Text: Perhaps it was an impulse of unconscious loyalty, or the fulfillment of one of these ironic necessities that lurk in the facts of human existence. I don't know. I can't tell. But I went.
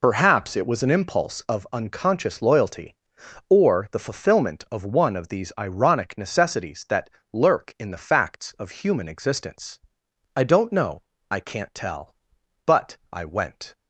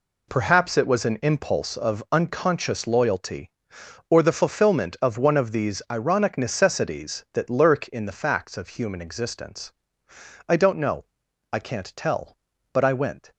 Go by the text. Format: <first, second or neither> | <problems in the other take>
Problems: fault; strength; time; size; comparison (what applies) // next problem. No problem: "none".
second | loses the start of "Perhaps"; at 0.0 s; 50 ms // pauses between "that" and "lurk"; slight; at 7.0 s; 0.24 s long